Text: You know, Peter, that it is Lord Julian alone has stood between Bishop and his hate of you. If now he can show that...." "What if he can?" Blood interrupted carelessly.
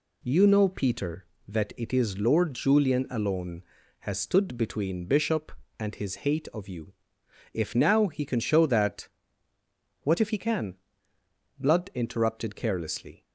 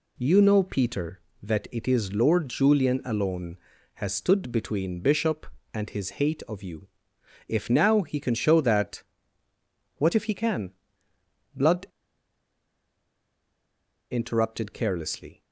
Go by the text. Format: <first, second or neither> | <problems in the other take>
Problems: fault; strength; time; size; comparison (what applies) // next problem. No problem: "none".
first | pauses between "Blood" and "interrupted"; strong; at 11.8 s; 2.2 s long